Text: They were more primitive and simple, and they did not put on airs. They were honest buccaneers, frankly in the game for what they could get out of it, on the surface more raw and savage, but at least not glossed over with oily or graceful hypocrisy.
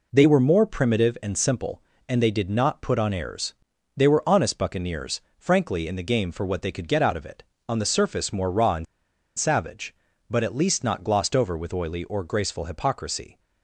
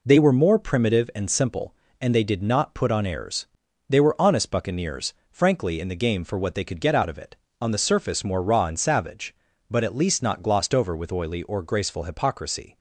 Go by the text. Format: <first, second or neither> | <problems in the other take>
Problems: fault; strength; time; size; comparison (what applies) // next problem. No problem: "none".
second | pauses between "and" and "savage"; noticeable; at 8.8 s; 0.53 s long